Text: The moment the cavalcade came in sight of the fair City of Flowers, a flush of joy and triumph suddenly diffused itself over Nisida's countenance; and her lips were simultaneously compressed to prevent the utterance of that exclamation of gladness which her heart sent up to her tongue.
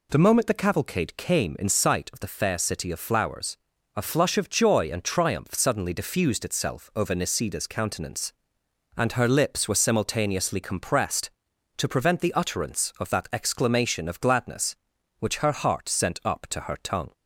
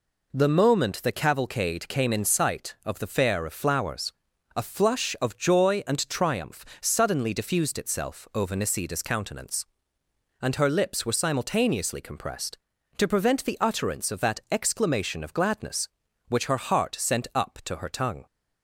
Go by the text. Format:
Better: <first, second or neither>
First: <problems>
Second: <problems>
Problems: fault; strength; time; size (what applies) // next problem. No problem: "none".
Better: first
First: none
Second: skips "City"; at 3.4 s // pauses between "triumph" and "suddenly"; slight; at 6.6 s; 0.16 s long